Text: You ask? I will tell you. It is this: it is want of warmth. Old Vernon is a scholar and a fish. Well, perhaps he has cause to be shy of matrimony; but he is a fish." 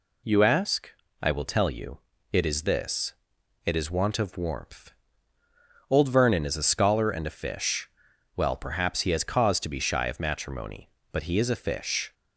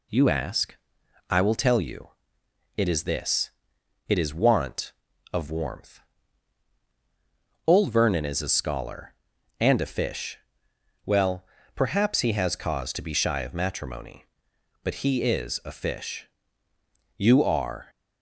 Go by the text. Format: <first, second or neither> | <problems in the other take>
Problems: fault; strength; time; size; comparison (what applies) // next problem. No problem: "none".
first | goes on to say "You are"; noticeable; from 17.1 s on; 0.70 s long